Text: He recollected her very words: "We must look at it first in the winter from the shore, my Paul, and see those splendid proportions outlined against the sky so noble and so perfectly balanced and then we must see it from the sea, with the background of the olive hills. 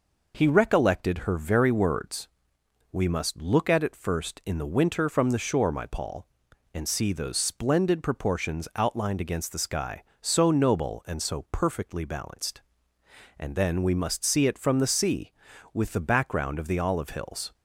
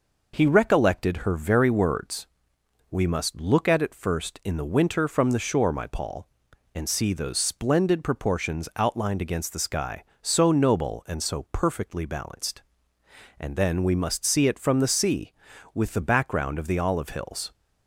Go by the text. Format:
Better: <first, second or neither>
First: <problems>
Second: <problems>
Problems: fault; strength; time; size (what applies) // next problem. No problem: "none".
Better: neither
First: none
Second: none